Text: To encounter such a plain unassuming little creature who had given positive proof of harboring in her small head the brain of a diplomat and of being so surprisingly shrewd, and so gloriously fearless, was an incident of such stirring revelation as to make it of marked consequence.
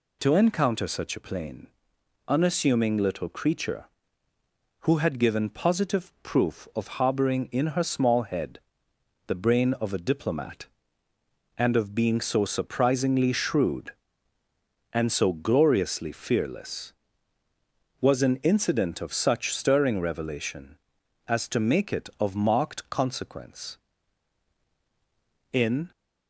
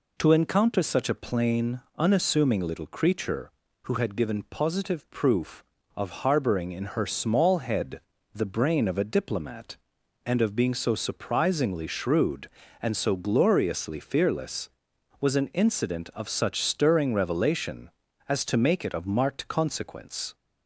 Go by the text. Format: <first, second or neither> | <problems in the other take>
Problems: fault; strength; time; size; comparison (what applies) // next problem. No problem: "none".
second | pauses between "plain" and "unassuming"; noticeable; at 1.6 s; 0.60 s long; slight in the second // pauses between "head" and "the"; noticeable; at 8.5 s; 0.70 s long; slight in the second // goes on to say "In"; slight; from 25.5 s on; 0.38 s long